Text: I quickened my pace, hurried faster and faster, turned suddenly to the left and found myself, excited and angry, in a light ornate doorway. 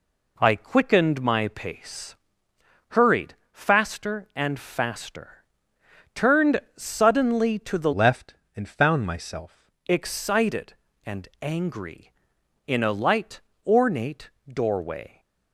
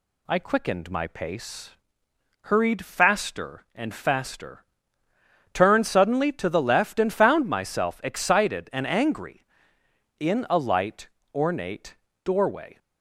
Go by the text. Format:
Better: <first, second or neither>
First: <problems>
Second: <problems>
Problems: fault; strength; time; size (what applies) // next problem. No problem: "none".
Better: second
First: pauses between "hurried" and "faster"; slight; at 3.3 s; 0.20 s long // pauses between "turned" and "suddenly"; slight; at 6.6 s; 0.16 s long // changes voice from "left" to "myself"; from 7.9 to 9.7 s; 1.8 s long // pauses between "light" and "ornate"; slight; at 13.4 s; 0.24 s long // pauses between "ornate" and "doorway"; slight; at 14.2 s; 0.18 s long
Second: pauses between "light" and "ornate"; slight; at 11.0 s; 0.26 s long // pauses between "ornate" and "doorway"; slight; at 11.9 s; 0.28 s long